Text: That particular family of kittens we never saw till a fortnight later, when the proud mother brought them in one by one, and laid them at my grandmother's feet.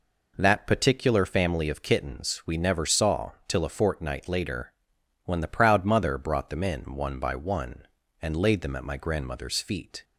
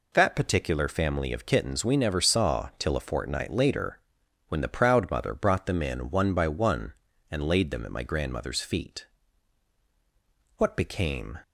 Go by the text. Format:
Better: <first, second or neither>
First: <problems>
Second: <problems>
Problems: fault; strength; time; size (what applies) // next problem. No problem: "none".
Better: first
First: none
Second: goes on to say "What became"; noticeable; from 10.5 s on; 0.82 s long